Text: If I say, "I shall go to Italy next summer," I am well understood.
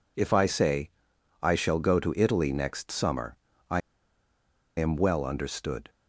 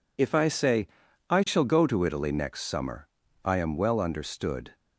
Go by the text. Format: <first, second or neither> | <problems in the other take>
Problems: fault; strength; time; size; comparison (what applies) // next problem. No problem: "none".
second | pauses between "I" and "am"; at 3.8 s; 0.98 s long